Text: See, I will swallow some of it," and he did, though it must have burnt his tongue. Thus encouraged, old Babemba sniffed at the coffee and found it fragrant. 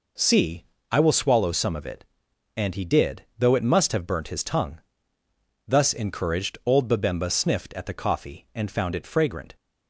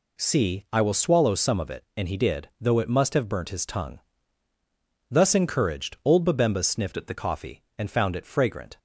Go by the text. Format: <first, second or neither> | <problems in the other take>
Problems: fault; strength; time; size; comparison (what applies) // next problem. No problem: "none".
first | changes voice from "at" to "the"; from 6.9 to 7.1 s; 0.2 s long